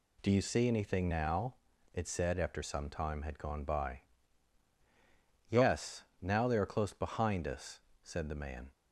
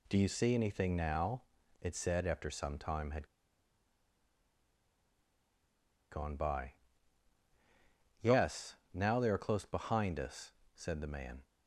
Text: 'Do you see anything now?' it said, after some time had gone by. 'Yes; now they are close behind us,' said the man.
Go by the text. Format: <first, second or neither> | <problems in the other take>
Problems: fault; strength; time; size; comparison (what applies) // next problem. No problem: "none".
first | pauses between "had" and "gone"; strong; at 3.2 s; 2.8 s long